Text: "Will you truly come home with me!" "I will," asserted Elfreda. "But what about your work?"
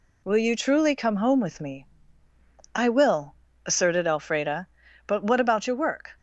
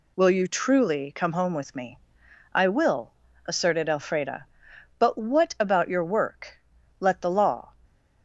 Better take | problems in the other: first | goes on to say "Let the law"; noticeable; from 6.9 s on; 0.76 s long

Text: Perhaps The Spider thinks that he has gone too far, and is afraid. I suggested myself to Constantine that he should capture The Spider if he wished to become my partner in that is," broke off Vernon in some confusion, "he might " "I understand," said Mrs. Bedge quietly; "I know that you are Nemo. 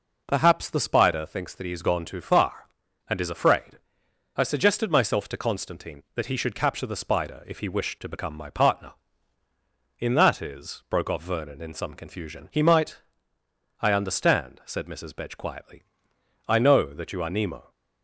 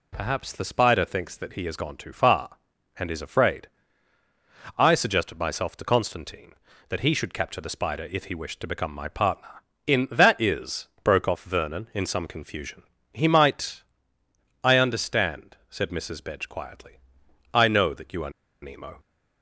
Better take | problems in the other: first | pauses between "are" and "Nemo"; slight; at 18.2 s; 0.32 s long

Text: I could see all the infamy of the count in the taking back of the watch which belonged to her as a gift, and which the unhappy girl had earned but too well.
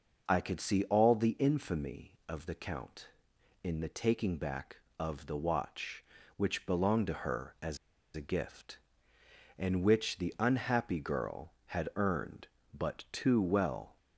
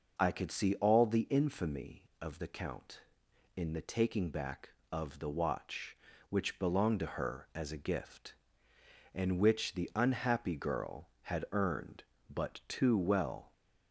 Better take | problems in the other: second | pauses between "as" and "a"; at 7.7 s; 0.36 s long

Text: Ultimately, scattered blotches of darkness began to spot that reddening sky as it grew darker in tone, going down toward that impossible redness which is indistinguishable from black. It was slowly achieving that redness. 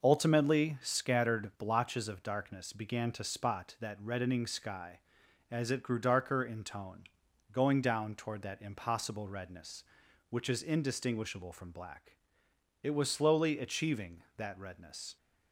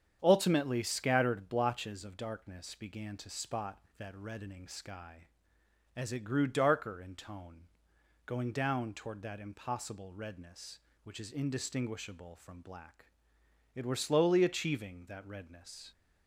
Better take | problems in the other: first | starts louder than the rest; strong; until 1.2 s; 8.5 dB // says "were" for "was"; at 13.8 s

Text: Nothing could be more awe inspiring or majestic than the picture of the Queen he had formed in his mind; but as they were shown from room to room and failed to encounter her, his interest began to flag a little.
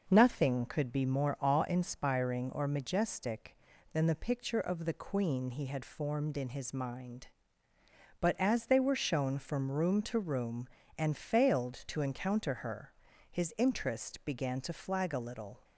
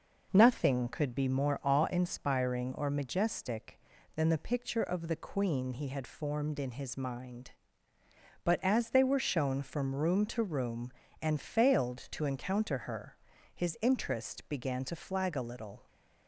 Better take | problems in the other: neither | none

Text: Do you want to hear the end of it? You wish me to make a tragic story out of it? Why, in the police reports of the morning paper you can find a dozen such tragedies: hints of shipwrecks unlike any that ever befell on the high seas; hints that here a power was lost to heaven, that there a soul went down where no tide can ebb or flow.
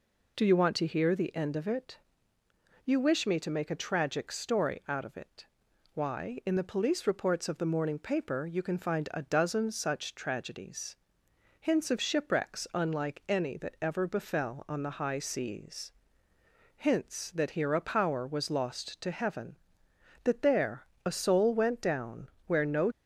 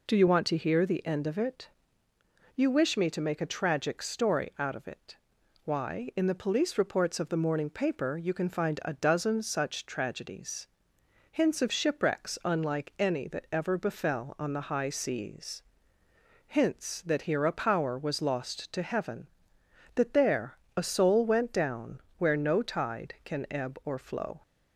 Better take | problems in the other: second | pauses between "there" and "a"; slight; at 20.8 s; 0.18 s long; slight in the second // pauses between "down" and "where"; slight; at 22.2 s; 0.20 s long; slight in the second // stops before "tide can ebb or flow"; at 22.9 s

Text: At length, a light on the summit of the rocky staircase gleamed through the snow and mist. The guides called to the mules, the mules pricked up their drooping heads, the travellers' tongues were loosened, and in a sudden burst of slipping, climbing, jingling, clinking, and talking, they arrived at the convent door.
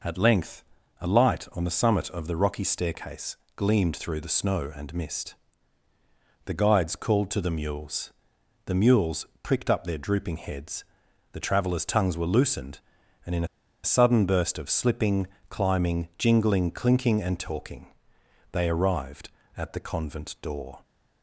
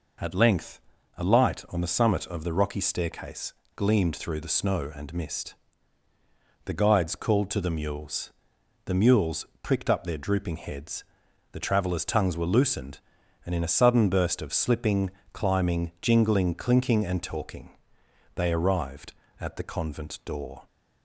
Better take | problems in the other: second | pauses between "staircase" and "gleamed"; slight; at 3.3 s; 0.18 s long; slight in the second // pauses between "mules" and "pricked"; slight; at 9.2 s; 0.18 s long; slight in the second // pauses between "in" and "a"; at 13.4 s; 0.39 s long

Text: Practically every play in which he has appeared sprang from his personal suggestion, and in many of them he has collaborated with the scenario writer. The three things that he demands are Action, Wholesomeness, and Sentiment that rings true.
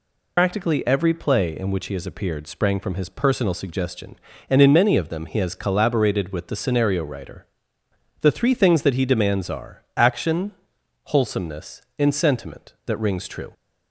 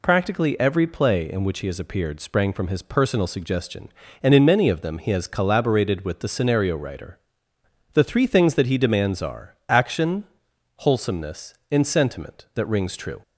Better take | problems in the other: second | loses the start of "Practically"; at 0.3 s; 90 ms

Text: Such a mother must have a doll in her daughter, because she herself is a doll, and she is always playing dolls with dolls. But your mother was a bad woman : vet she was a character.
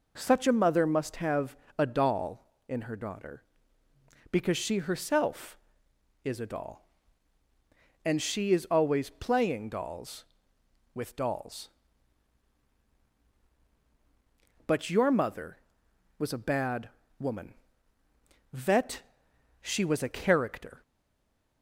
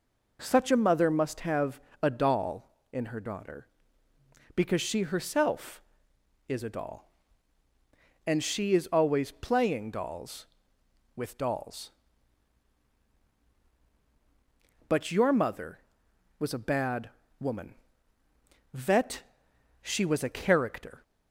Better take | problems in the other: second | pauses between "have" and "a"; slight; at 1.5 s; 0.22 s long; slight in the second // pauses between "bad" and "woman"; slight; at 16.8 s; 0.32 s long; slight in the second // pauses between "vet" and "she"; noticeable; at 19.0 s; 0.60 s long; noticeable in the second // stays silent after the last word; slight; from 20.8 s on; 0.8 s long

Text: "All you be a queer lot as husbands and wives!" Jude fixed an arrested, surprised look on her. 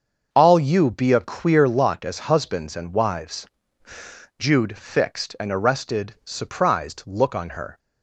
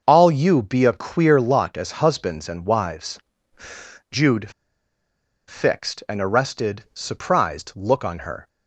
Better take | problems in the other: first | starts louder than the rest; until 1.0 s; 6.5 dB; also in the first // pauses between "Jude" and "fixed"; noticeable; at 4.5 s; 0.97 s long

